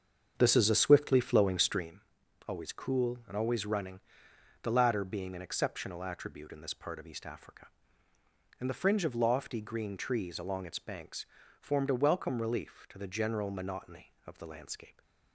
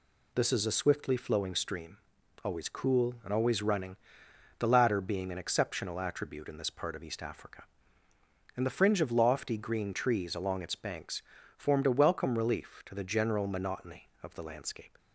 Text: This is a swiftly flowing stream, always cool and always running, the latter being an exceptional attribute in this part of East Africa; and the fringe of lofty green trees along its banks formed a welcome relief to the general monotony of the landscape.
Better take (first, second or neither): second